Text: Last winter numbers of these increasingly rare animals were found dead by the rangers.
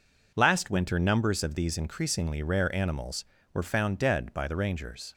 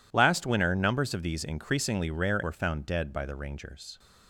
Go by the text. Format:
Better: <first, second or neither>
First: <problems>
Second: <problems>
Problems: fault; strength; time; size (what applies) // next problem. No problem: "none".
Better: first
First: none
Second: skips "animals"; at 2.4 s